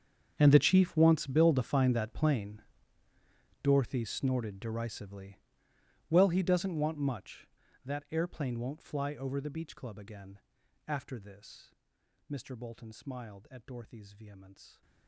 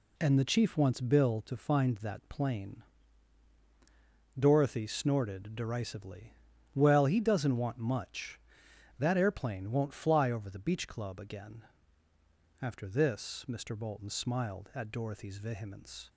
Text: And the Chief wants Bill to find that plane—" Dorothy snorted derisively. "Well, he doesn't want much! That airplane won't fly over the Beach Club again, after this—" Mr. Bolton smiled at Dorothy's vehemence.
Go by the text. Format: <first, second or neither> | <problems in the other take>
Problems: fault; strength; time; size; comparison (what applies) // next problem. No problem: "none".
second | gets quieter; strong; throughout; 20 dB